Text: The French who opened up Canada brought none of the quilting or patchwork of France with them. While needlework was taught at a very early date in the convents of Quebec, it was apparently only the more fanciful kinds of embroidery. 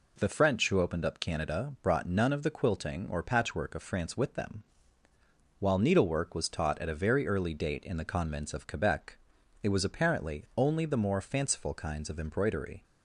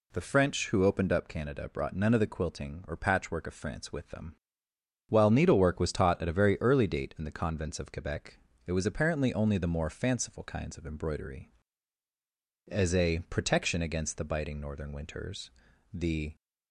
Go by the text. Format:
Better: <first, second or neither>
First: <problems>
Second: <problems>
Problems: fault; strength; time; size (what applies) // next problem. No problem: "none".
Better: first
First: none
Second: goes on to say "As a protection against the biting northern winters the"; strong; from 12.6 s on; 3.6 s long